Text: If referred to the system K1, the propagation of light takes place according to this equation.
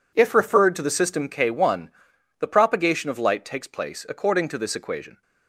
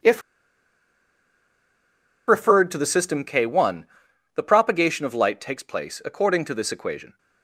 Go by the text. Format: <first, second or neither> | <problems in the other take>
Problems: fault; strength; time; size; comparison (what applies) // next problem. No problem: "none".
first | pauses between "If" and "referred"; strong; at 0.2 s; 2.0 s long